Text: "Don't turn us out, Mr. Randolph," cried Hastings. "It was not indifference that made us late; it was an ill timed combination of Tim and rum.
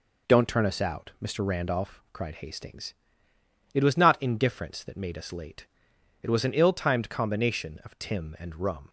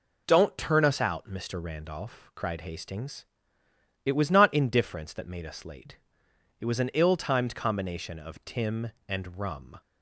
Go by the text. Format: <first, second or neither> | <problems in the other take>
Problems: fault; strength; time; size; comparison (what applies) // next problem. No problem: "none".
neither | none